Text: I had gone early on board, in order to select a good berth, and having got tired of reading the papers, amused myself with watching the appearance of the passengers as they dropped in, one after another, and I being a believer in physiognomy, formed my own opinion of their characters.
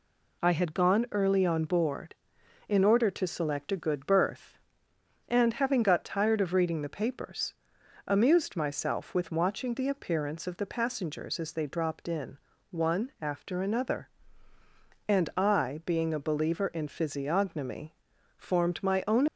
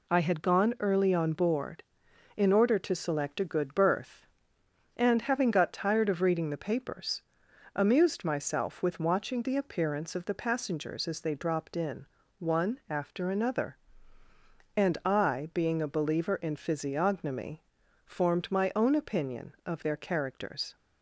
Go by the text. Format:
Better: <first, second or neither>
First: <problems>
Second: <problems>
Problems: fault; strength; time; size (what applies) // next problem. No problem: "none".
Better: second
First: stops before "opinion of their characters"; at 19.2 s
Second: none